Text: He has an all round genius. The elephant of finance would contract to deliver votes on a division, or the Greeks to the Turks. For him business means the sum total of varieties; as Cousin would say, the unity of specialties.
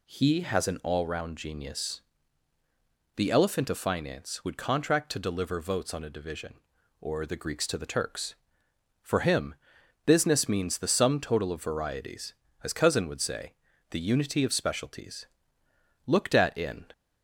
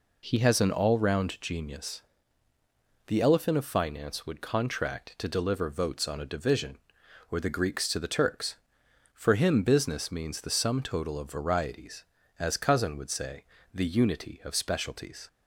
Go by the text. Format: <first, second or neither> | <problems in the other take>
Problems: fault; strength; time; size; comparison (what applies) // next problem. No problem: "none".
second | pauses between "him" and "business"; noticeable; at 9.5 s; 0.50 s long // goes on to say "Looked at in"; noticeable; from 16.0 s on; 0.84 s long